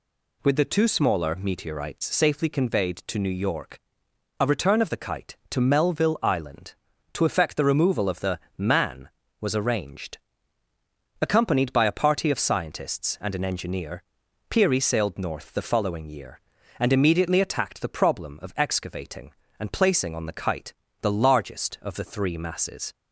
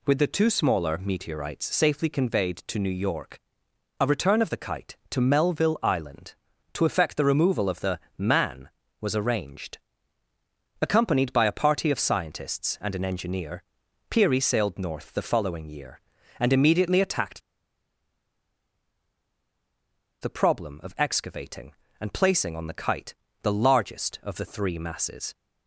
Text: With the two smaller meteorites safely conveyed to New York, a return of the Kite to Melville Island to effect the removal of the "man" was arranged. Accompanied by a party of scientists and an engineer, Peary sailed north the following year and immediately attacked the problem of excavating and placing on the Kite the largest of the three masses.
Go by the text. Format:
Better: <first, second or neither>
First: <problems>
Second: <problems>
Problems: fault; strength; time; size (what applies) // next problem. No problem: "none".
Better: first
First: pauses between "the" and "man"; slight; at 8.3 s; 0.18 s long // pauses between "Kite" and "the"; slight; at 20.7 s; 0.28 s long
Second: pauses between "the" and "man"; slight; at 7.9 s; 0.18 s long // pauses between "attacked" and "the"; strong; at 17.3 s; 2.8 s long // pauses between "Kite" and "the"; slight; at 23.1 s; 0.28 s long